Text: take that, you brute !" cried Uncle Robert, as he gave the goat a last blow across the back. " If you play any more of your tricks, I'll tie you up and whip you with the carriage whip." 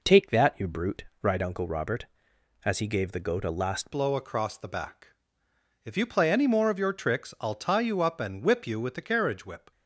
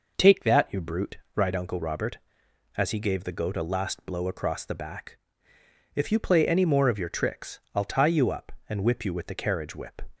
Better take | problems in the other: second | changes voice at "blow"; from 3.9 s on; 5.8 s long

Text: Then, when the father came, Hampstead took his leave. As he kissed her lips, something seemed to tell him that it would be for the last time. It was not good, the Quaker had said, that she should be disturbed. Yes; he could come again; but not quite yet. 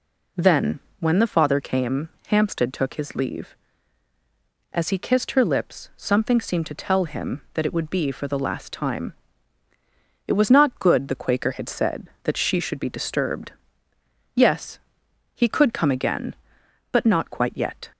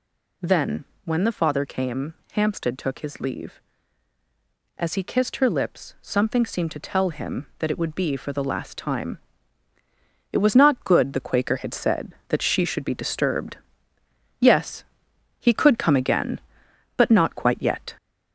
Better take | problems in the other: first | gets louder; slight; throughout; 3 dB

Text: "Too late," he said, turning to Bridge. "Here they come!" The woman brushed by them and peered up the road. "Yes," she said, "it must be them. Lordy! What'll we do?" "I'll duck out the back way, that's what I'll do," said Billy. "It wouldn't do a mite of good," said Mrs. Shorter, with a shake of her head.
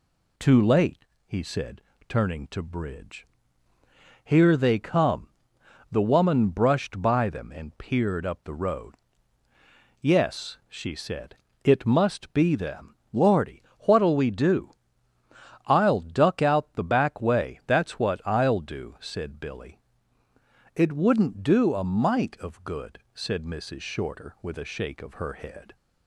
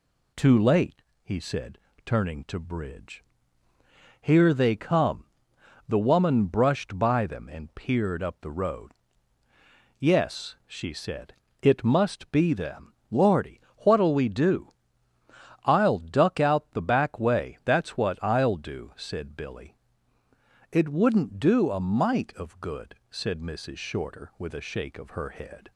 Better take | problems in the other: neither | none

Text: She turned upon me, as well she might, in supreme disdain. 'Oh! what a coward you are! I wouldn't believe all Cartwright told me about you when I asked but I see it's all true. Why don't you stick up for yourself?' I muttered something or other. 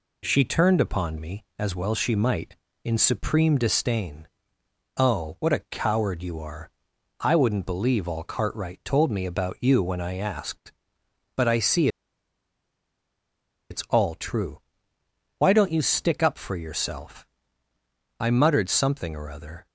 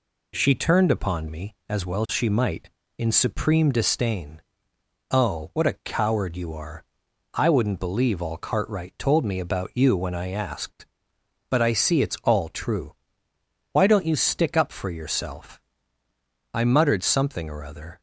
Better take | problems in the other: second | pauses between "see" and "it's"; strong; at 11.8 s; 1.8 s long

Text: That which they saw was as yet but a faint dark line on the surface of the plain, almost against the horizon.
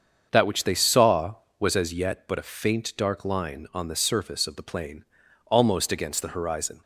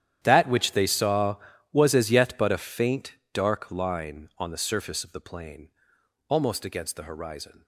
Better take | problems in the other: first | gets quieter; strong; throughout; 18.5 dB // starts louder than the rest; strong; until 1.2 s; 10.5 dB; also in the first // pauses between "faint" and "dark"; slight; at 3.1 s; 0.20 s long

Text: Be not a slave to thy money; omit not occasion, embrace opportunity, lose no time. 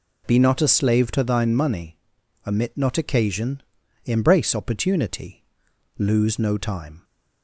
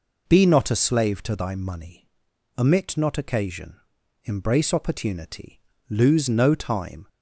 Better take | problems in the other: second | says "thine" for "thy"; at 1.2 s

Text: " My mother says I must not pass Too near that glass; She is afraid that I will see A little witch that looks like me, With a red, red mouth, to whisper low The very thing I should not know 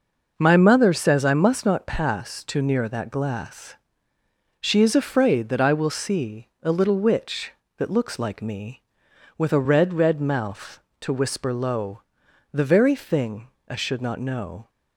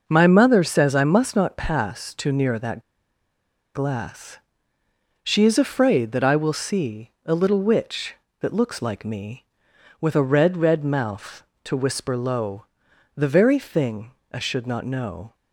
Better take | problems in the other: first | pauses between "that" and "glass"; noticeable; at 2.8 s; 0.94 s long // pauses between "low" and "The"; noticeable; at 12.6 s; 0.50 s long; noticeable in the first // pauses between "thing" and "I"; slight; at 14.1 s; 0.22 s long; slight in the first

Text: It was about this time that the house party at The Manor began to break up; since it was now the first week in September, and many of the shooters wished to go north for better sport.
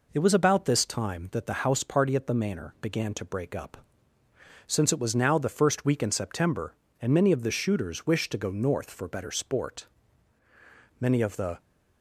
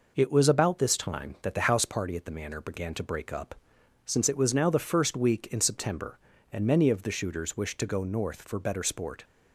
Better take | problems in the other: second | goes on to say "Many of the"; from 10.9 s on; 0.60 s long

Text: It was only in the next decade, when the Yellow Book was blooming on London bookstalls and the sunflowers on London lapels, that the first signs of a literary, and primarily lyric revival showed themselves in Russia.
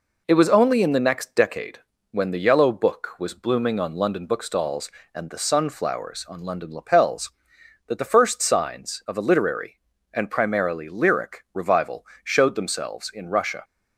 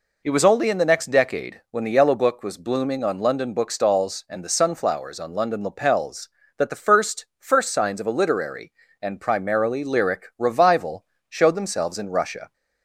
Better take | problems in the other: first | says "first" twice; at 7.4 s // pauses between "revival" and "showed"; slight; at 11.0 s; 0.24 s long; slight in the first

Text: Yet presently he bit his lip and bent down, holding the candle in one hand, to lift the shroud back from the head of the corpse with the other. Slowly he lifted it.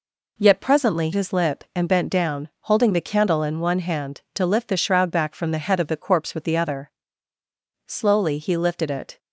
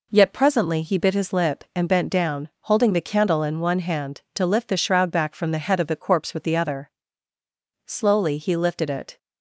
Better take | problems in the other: second | skips "he bit"; at 1.1 s

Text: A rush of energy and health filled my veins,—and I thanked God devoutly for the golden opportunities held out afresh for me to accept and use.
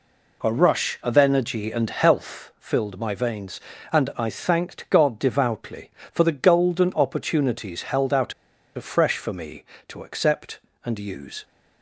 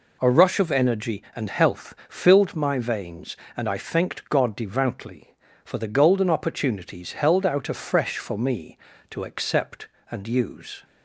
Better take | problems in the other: second | pauses between "out" and "afresh"; at 8.3 s; 0.42 s long

